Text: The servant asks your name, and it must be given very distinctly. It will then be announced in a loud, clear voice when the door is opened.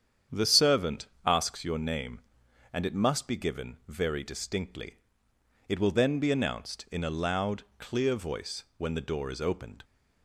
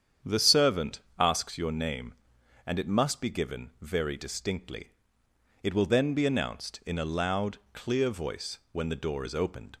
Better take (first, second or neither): neither